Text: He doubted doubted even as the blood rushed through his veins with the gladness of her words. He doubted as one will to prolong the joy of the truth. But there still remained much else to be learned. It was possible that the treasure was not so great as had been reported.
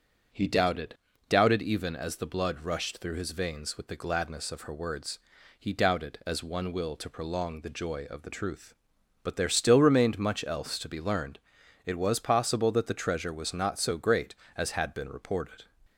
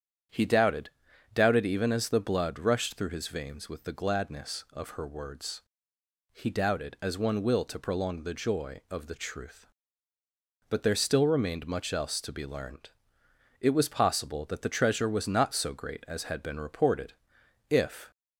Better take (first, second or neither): first